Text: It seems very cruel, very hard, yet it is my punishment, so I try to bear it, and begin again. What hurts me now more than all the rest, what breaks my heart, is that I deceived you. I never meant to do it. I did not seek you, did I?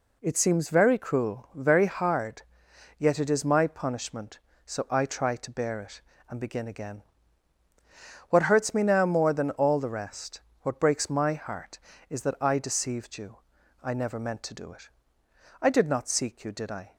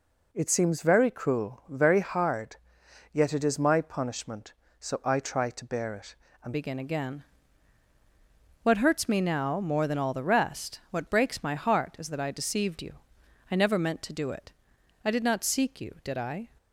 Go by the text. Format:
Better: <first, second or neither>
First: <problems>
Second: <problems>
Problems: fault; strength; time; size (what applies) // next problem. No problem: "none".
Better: first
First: none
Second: changes voice at "begin"; from 6.5 s on; 9.9 s long